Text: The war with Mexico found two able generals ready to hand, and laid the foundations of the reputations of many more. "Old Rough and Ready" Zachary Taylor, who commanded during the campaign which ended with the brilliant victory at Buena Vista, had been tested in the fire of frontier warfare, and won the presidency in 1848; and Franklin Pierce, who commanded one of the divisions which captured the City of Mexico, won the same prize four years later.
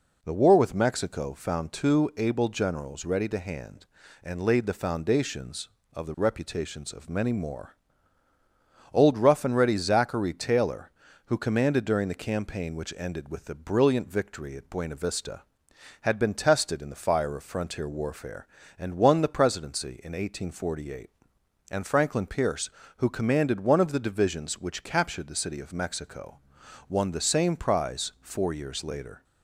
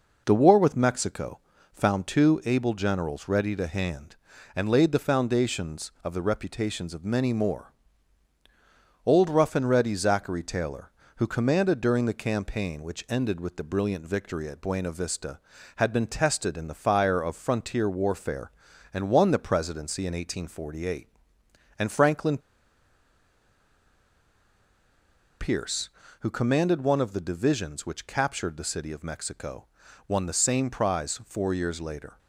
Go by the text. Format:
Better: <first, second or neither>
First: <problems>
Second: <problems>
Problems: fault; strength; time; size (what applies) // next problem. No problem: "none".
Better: first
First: none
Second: pauses between "Mexico" and "found"; slight; at 1.3 s; 0.32 s long // pauses between "Franklin" and "Pierce"; strong; at 22.3 s; 3.0 s long